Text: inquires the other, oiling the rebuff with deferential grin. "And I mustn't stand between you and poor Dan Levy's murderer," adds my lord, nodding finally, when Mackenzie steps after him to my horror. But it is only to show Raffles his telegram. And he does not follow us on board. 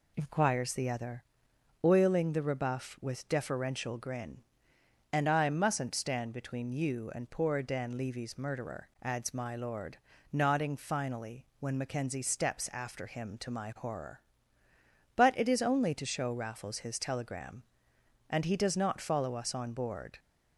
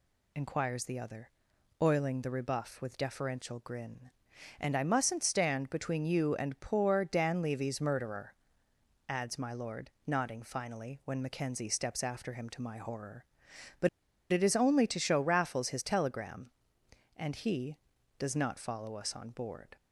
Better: first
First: none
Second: pauses between "But" and "it"; at 13.8 s; 0.43 s long

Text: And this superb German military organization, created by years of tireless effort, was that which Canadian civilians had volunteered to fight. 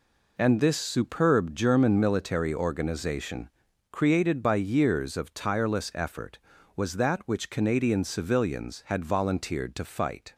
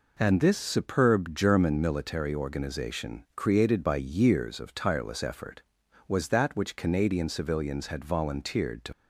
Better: first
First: none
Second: stops before "fight"; at 8.9 s

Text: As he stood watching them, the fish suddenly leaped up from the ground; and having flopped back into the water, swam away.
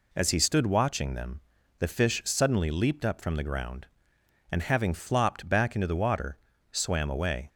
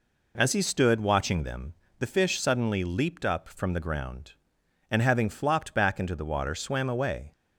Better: neither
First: none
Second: none

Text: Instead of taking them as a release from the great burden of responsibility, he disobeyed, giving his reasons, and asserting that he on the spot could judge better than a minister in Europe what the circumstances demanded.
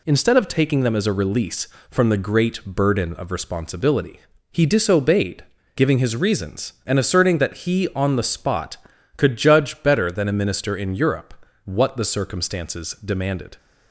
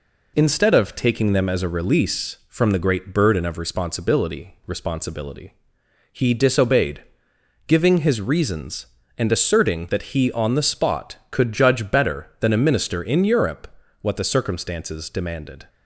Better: first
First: pauses between "Europe" and "what"; slight; at 11.3 s; 0.30 s long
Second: says "responsibility" twice; at 4.6 s // pauses between "Europe" and "what"; slight; at 13.7 s; 0.28 s long

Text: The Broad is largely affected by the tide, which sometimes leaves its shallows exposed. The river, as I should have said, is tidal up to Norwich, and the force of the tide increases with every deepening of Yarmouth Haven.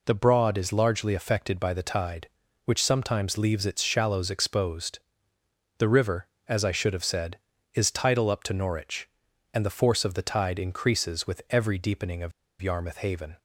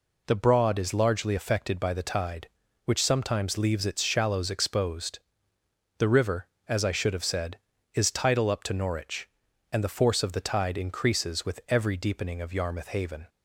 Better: second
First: pauses between "of" and "Yarmouth"; slight; at 12.3 s; 0.30 s long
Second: none

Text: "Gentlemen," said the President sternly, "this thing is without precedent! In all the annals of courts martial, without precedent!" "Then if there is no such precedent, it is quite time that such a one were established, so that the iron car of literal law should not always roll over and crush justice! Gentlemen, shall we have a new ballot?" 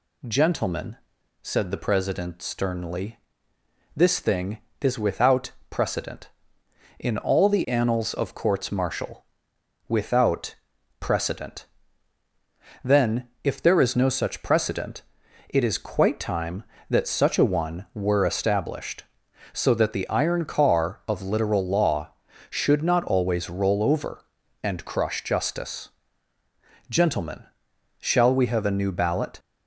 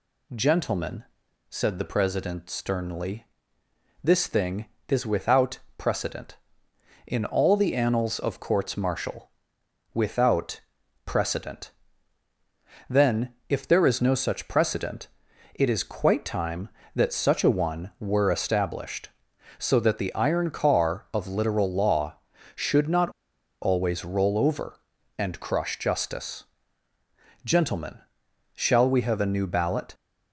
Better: first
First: pauses between "without" and "precedent"; slight; at 5.5 s; 0.18 s long // pauses between "without" and "precedent"; at 10.5 s; 0.44 s long // pauses between "Then" and "if"; slight; at 13.2 s; 0.16 s long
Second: pauses between "without" and "precedent"; slight; at 5.5 s; 0.18 s long // pauses between "without" and "precedent"; at 10.6 s; 0.44 s long // pauses between "Then" and "if"; slight; at 13.3 s; 0.16 s long // pauses between "not" and "always"; noticeable; at 23.1 s; 0.51 s long

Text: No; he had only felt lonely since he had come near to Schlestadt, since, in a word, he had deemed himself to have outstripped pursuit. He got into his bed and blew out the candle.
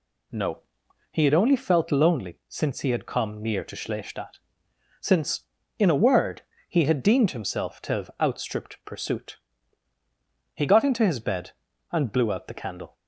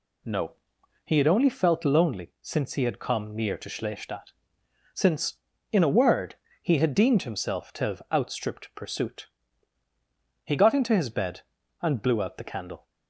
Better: neither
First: none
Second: none

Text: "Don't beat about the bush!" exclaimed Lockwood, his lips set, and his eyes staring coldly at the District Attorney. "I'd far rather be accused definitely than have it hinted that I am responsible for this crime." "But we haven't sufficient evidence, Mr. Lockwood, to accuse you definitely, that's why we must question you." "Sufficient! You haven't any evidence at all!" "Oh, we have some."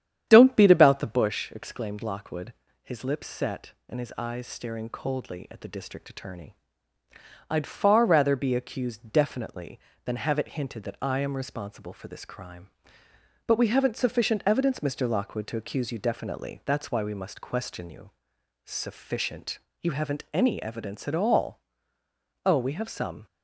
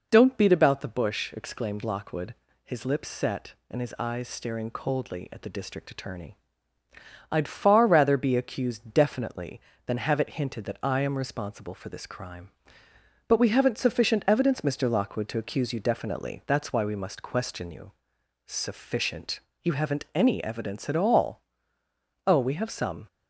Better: second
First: starts louder than the rest; strong; until 1.4 s; 9.5 dB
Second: none

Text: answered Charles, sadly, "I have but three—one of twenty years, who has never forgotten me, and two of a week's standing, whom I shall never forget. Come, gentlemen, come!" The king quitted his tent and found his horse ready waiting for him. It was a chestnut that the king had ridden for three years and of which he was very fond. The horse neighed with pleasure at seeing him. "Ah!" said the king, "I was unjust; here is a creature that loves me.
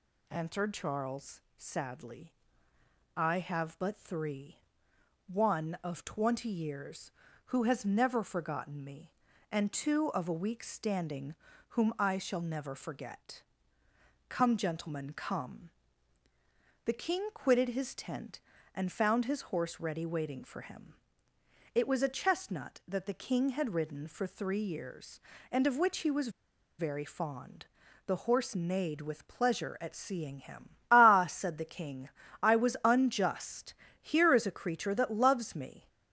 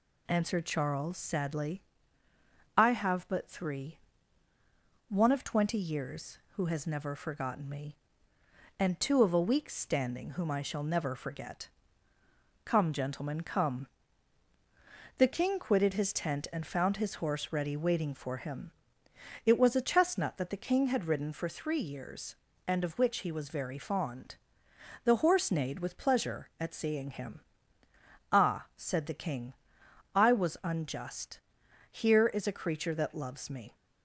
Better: second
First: pauses between "was" and "very"; noticeable; at 26.2 s; 0.49 s long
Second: none

